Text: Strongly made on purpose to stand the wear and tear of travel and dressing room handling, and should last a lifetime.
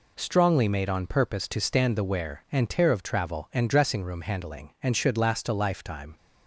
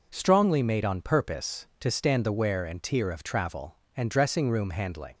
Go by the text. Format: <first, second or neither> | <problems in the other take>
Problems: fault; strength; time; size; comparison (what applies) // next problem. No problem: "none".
first | stops before "and should last a lifetime"; at 5.1 s